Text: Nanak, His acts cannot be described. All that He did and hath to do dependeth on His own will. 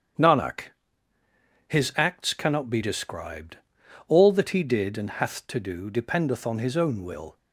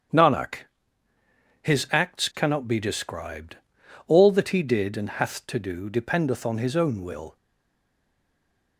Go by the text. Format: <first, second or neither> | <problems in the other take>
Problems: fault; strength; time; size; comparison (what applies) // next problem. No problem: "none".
first | starts louder than the rest; strong; until 2.2 s; 8.5 dB; strong in the first // stays silent after the last word; noticeable; from 7.3 s on; 1.4 s long